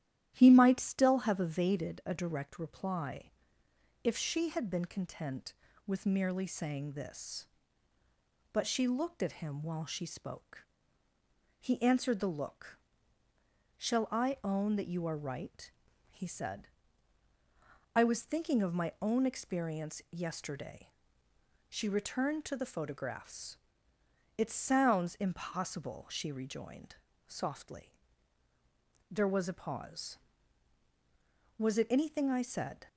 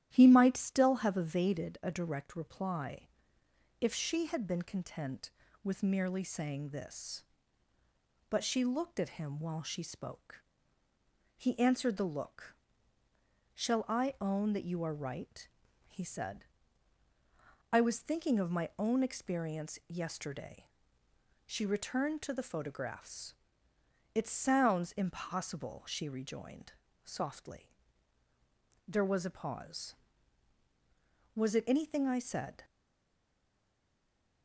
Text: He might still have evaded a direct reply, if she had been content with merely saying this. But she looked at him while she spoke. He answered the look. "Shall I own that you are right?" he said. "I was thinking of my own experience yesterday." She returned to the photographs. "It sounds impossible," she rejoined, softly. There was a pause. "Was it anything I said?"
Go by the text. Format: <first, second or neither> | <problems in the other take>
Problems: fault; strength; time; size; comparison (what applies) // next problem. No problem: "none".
first | starts louder than the rest; strong; until 1.1 s; 12 dB; strong in the first // stays silent after the last word; noticeable; from 32.6 s on; 1.8 s long